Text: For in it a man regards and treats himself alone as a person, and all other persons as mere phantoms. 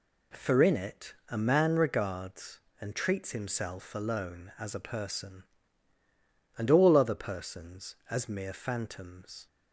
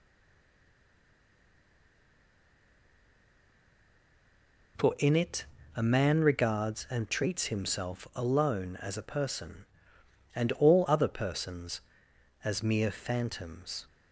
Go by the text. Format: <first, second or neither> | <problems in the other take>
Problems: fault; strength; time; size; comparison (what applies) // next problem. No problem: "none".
first | stays silent before the first word; strong; until 4.7 s; 4.7 s long // pauses between "it" and "a"; slight; at 5.4 s; 0.28 s long